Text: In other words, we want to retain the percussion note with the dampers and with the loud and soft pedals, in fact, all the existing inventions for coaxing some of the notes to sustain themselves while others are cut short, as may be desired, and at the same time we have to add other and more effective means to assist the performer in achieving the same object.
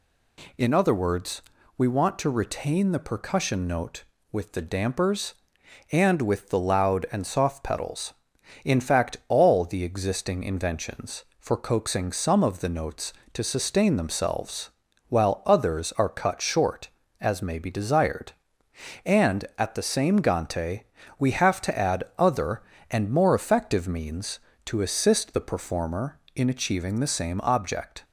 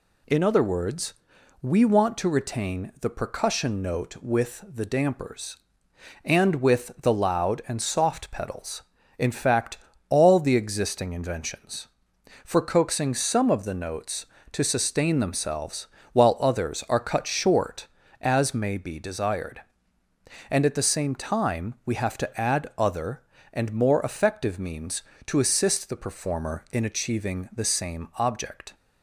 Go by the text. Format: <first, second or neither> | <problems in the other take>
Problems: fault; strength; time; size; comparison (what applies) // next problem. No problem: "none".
second | pauses between "themselves" and "while"; at 14.7 s; 0.38 s long; slight in the second // says "gante" for "time"; at 20.1 s